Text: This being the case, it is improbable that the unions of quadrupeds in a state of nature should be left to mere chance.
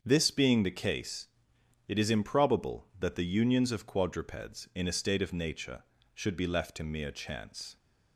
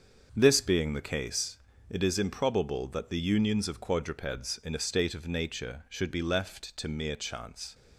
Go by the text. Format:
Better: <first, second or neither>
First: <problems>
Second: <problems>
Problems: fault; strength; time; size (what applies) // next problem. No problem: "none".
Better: neither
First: starts louder than the rest; until 1.0 s; 7 dB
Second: starts louder than the rest; until 1.3 s; 7 dB